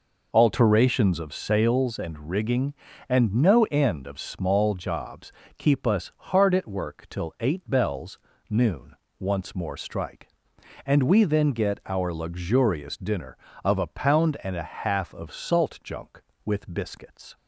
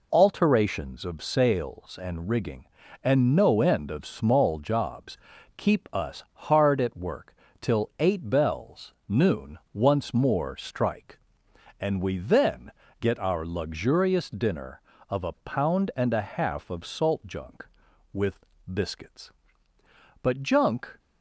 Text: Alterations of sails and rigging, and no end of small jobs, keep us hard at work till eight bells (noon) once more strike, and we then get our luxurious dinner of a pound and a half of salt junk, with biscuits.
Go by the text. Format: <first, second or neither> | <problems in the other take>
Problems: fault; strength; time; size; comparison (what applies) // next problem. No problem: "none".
first | pauses between "work" and "till"; slight; at 7.3 s; 0.26 s long // pauses between "then" and "get"; slight; at 12.7 s; 0.26 s long // pauses between "with" and "biscuits"; slight; at 18.3 s; 0.32 s long // goes on to say "But junk"; noticeable; from 20.2 s on; 0.78 s long